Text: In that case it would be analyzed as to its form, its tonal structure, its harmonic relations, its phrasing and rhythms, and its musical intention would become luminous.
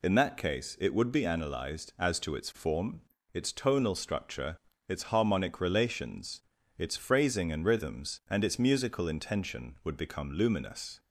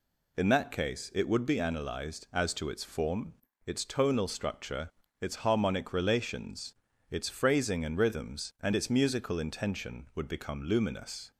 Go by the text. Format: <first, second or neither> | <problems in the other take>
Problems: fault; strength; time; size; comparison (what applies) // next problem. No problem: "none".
neither | none